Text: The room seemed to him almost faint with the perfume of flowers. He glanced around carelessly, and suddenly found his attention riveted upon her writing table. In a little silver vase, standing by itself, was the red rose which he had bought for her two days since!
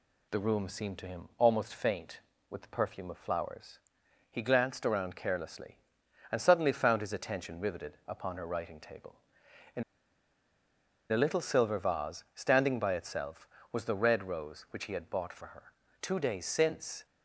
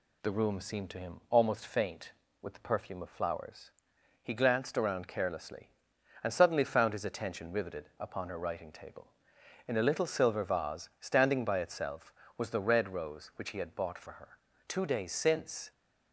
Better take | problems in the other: second | pauses between "In" and "a"; strong; at 9.8 s; 1.2 s long // pauses between "her" and "two"; slight; at 15.7 s; 0.28 s long; slight in the second

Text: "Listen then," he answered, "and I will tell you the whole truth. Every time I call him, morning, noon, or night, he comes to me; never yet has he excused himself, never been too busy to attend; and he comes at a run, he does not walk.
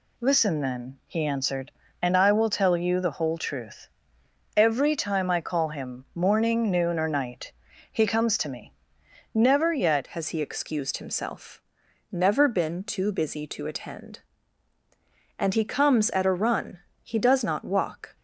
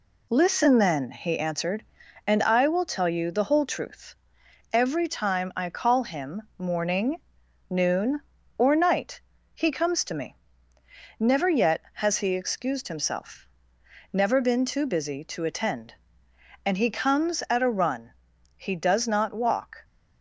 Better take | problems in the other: second | changes voice at "has"; from 10.0 s on; 8.1 s long

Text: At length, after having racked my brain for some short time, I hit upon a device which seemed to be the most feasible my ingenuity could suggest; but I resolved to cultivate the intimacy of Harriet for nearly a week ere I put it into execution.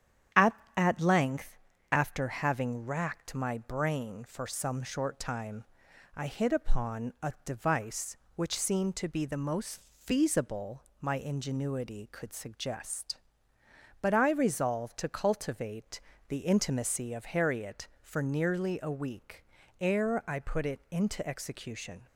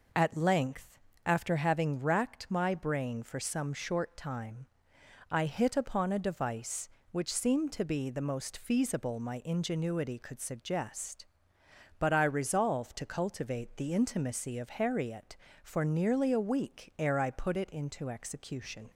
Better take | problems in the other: second | starts louder than the rest; strong; until 1.5 s; 9.5 dB // says "At" twice; at 0.7 s // pauses between "most" and "feasible"; slight; at 9.7 s; 0.18 s long // pauses between "feasible" and "my"; slight; at 10.8 s; 0.20 s long // pauses between "cultivate" and "the"; slight; at 15.9 s; 0.28 s long // pauses between "week" and "ere"; at 19.4 s; 0.38 s long

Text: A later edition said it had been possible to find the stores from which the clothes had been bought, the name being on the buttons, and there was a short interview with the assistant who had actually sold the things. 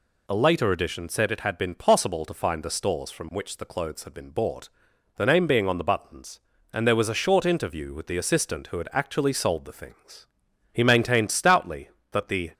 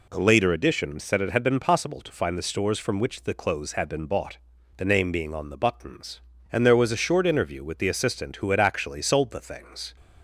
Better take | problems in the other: second | goes on to say "He maintained stoutly that the"; strong; from 10.7 s on; 1.7 s long

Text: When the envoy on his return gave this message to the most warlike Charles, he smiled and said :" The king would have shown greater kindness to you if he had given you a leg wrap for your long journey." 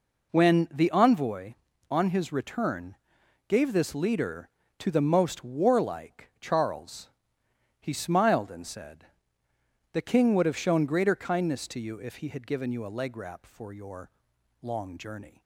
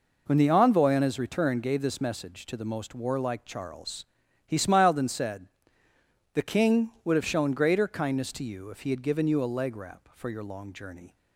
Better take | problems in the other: second | pauses between "return" and "gave"; noticeable; at 2.9 s; 0.52 s long // says "leader" for "message"; at 3.9 s // pauses between "your" and "long"; noticeable; at 14.1 s; 0.50 s long

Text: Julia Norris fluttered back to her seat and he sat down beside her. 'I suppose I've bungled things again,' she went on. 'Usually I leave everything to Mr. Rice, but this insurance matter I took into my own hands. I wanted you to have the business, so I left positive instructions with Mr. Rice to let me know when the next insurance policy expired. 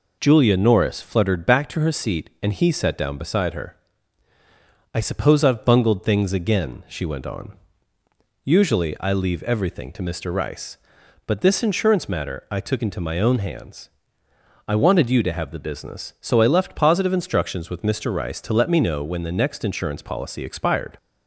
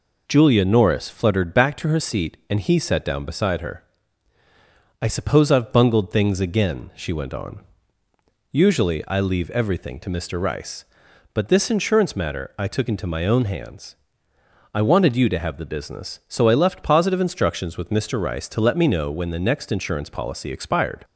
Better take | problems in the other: neither | none

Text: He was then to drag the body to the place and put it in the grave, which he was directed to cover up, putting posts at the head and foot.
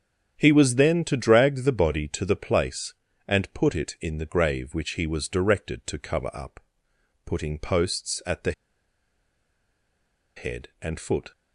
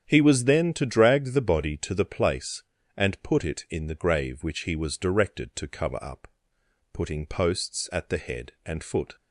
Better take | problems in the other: second | starts louder than the rest; strong; until 1.4 s; 9 dB; strong in the second // pauses between "the" and "head"; strong; at 8.5 s; 1.8 s long

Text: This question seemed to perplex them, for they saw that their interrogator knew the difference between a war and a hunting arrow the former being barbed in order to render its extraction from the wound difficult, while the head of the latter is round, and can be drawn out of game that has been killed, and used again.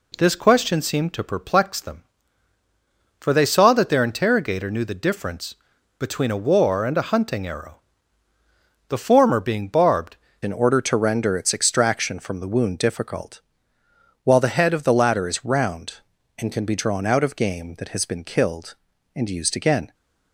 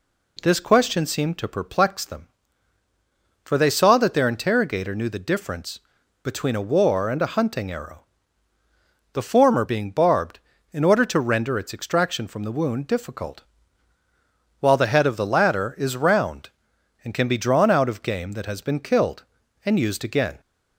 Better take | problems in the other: second | pauses between "difference" and "between"; at 5.5 s; 0.42 s long; also in the second // pauses between "arrow" and "the"; at 7.7 s; 1.1 s long; also in the second // changes voice at "in"; from 10.4 s on; 9.5 s long

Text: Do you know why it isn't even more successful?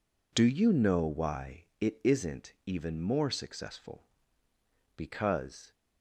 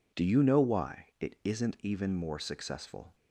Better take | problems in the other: second | goes on to say "Because"; noticeable; from 4.9 s on; 0.78 s long

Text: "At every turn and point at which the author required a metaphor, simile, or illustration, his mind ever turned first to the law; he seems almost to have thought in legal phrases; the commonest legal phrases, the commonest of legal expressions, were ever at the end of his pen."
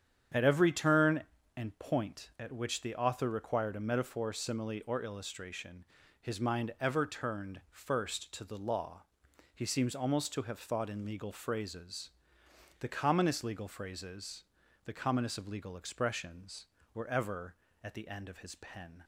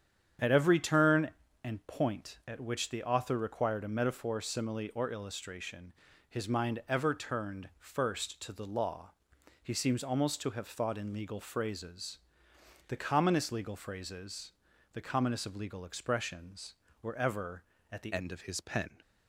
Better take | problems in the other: first | starts louder than the rest; strong; until 1.7 s; 8.5 dB; strong in the first // changes voice at "end"; from 18.1 s on; 0.8 s long

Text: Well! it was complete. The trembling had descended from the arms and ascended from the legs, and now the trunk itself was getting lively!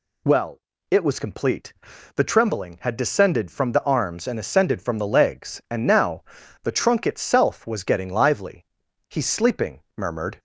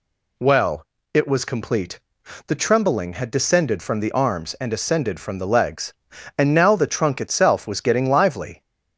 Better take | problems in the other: second | pauses between "now" and "the"; at 6.2 s; 0.39 s long // goes on to say "He's sleeping murmured"; noticeable; from 9.0 s on; 1.3 s long

